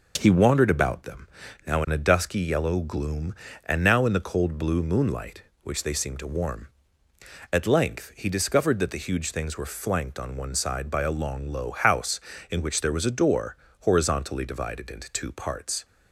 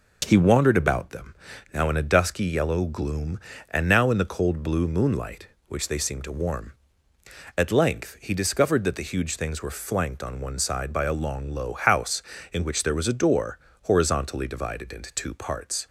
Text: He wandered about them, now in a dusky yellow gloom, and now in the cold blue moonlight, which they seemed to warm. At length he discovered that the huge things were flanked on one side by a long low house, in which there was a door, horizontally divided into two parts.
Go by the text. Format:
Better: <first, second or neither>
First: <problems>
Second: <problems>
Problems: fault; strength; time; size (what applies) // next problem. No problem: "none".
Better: neither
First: none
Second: none